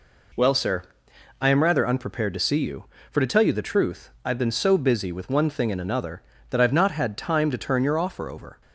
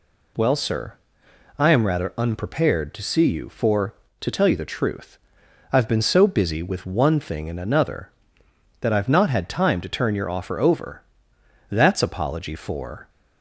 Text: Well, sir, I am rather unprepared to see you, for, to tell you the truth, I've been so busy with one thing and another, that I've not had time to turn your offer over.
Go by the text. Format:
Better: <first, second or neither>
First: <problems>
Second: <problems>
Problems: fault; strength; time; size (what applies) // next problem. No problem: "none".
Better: first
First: none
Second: goes on to say "That's apology for"; from 11.6 s on; 1.4 s long